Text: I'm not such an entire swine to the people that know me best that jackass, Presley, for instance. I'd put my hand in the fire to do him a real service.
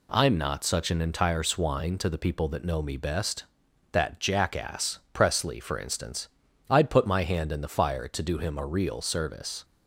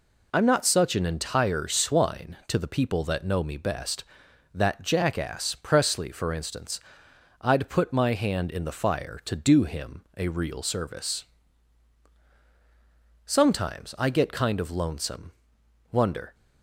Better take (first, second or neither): first